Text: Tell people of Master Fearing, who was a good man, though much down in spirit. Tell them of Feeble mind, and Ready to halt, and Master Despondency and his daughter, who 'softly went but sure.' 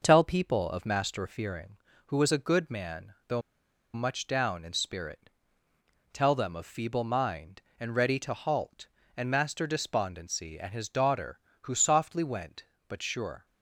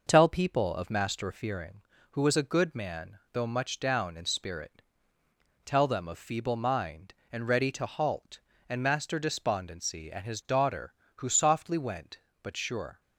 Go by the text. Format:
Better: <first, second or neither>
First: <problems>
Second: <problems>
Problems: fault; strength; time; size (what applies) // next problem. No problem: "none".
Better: second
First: pauses between "though" and "much"; noticeable; at 3.4 s; 0.52 s long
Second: none